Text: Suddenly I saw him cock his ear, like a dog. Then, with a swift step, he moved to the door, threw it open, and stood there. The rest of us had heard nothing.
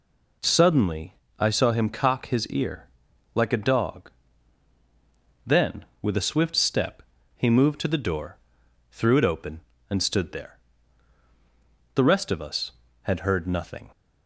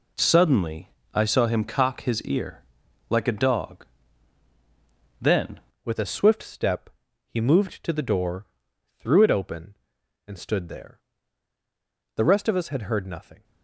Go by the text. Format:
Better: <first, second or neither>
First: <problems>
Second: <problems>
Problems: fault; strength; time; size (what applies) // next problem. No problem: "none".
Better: first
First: pauses between "Suddenly" and "I"; slight; at 1.1 s; 0.24 s long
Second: pauses between "Suddenly" and "I"; slight; at 0.8 s; 0.24 s long // changes voice at "with"; from 5.8 s on; 7.6 s long